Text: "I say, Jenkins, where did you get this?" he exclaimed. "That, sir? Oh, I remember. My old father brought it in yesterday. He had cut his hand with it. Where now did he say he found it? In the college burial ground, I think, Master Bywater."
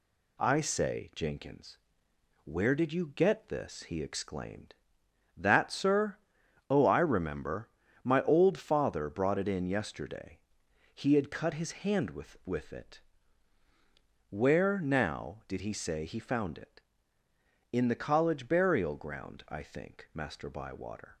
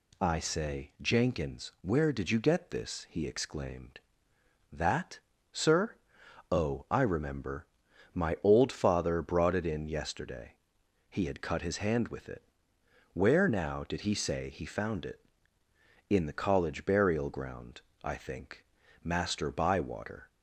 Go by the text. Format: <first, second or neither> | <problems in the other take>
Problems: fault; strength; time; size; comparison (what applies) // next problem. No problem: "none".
second | says "with" twice; at 12.4 s